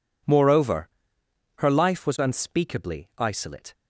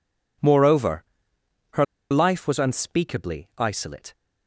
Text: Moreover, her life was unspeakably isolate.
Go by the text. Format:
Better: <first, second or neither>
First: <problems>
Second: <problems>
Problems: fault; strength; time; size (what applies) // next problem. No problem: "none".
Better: first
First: none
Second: pauses between "her" and "life"; slight; at 1.8 s; 0.26 s long